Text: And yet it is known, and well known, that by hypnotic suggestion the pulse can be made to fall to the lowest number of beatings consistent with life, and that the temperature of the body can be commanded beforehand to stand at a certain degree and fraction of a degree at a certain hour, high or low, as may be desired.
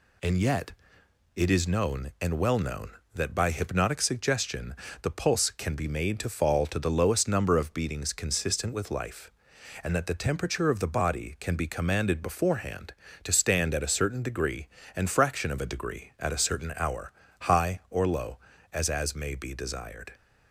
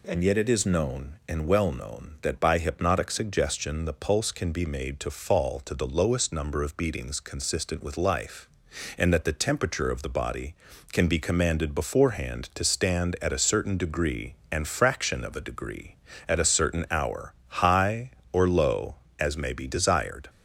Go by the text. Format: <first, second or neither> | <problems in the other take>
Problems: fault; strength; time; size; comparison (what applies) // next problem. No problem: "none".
second | pauses between "yet" and "it"; noticeable; at 0.7 s; 0.64 s long // pauses between "suggestion" and "the"; slight; at 4.7 s; 0.28 s long // says "as" twice; at 18.8 s